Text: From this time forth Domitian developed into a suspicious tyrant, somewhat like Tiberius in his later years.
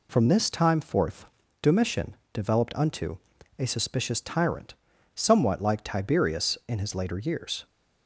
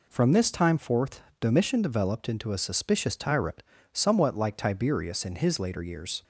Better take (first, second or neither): second